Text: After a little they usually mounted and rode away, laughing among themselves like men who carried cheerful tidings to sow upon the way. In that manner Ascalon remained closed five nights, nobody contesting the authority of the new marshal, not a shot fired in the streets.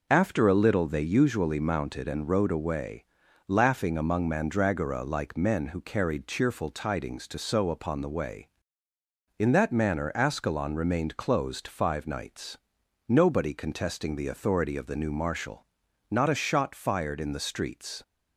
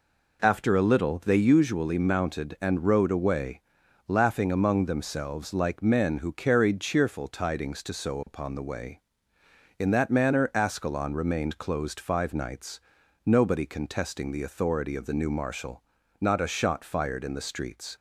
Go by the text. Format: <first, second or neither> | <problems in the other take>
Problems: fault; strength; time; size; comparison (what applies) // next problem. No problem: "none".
second | says "mandragora" for "themselves"; at 4.2 s